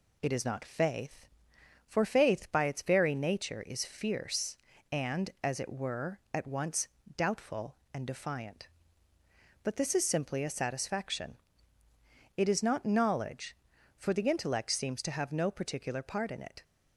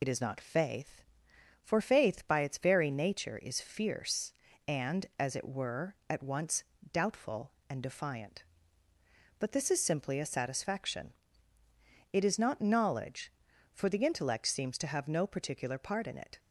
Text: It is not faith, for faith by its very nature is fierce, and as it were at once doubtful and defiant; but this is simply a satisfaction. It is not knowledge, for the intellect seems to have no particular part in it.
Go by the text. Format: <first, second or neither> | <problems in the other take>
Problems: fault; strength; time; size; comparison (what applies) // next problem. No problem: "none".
first | loses the start of "It"; at 0.0 s; 50 ms // pauses between "once" and "doubtful"; slight; at 6.6 s; 0.28 s long; slight in the first